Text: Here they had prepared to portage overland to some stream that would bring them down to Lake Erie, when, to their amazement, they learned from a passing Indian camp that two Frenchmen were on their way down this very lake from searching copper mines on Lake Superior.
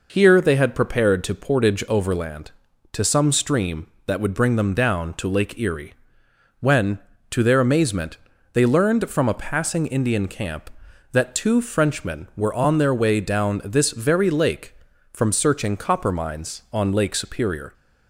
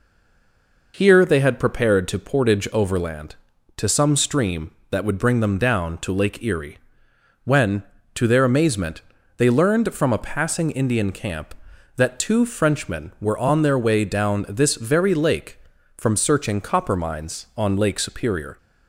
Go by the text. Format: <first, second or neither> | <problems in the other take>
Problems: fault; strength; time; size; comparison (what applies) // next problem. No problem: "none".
first | stays silent before the first word; slight; until 0.9 s; 0.9 s long